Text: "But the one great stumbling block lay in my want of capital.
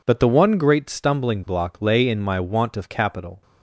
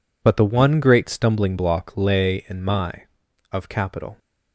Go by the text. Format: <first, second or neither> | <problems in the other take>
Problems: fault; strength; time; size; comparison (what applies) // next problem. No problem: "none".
first | skips "want"; at 3.2 s